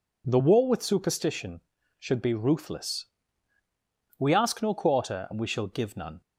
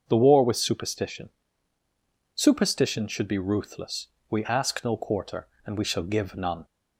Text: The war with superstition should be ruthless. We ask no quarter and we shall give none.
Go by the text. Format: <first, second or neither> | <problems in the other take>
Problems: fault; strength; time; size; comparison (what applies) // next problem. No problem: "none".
first | starts louder than the rest; until 1.0 s; 6.5 dB // says "superstition" twice; at 2.3 s